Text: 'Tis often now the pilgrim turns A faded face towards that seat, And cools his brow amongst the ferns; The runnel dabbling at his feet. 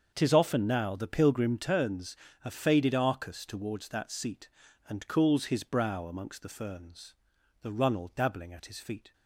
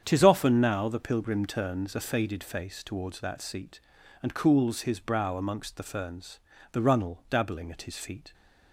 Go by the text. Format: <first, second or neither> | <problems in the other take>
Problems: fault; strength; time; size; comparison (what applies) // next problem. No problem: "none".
second | starts louder than the rest; until 1.1 s; 6.5 dB; strong in the second // pauses between "turns" and "A"; slight; at 2.1 s; 0.26 s long // says "arcus" for "face"; at 2.9 s